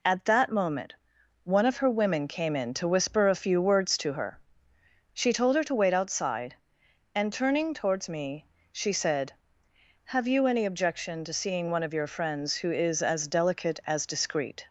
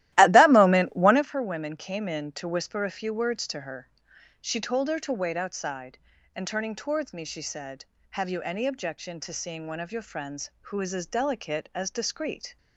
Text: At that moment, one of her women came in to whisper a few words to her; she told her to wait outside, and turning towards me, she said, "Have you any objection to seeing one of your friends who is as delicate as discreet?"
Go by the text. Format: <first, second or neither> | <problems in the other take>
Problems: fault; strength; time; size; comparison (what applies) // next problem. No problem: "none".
first | starts louder than the rest; strong; until 1.2 s; 15 dB